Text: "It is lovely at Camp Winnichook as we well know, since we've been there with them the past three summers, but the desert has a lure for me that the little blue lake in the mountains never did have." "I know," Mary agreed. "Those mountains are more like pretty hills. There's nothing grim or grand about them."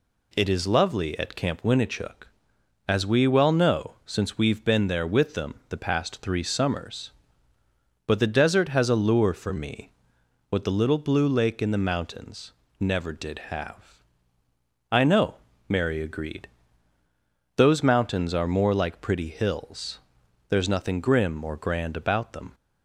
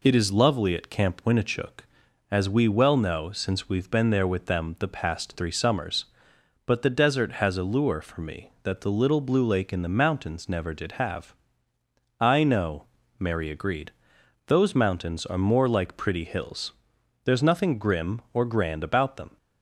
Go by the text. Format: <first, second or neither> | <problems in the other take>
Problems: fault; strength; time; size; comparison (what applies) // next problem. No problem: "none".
second | says "what" for "that"; at 10.4 s // pauses between "mountains" and "never"; slight; at 12.5 s; 0.28 s long